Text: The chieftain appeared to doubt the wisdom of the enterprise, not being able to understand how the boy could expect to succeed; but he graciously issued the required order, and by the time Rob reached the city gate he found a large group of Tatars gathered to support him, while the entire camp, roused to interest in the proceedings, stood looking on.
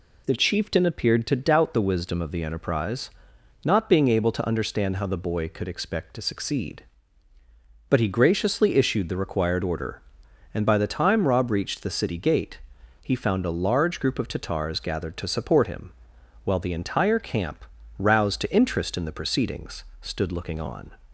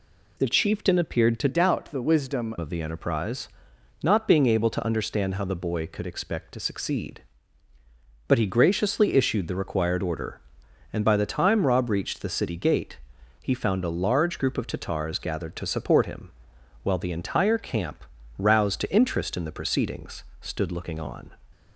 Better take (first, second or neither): first